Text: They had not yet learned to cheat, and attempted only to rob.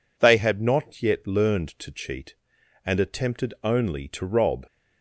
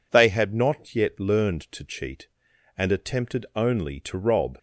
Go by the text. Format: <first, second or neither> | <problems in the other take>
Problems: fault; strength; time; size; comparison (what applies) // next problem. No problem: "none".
neither | none